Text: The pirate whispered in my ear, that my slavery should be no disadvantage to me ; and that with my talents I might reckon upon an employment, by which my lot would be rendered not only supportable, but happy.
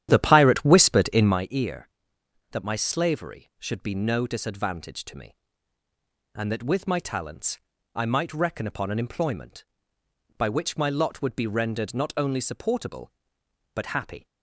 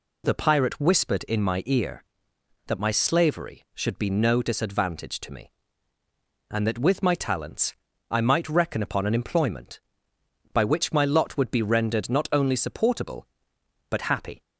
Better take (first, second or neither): second